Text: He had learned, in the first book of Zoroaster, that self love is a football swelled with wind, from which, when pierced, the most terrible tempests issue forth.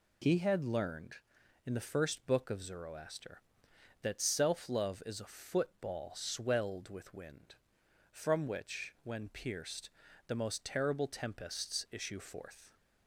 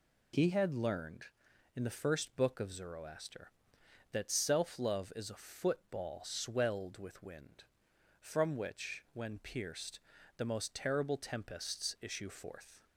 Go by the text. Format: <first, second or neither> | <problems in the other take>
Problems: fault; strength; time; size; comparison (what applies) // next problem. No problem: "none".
neither | none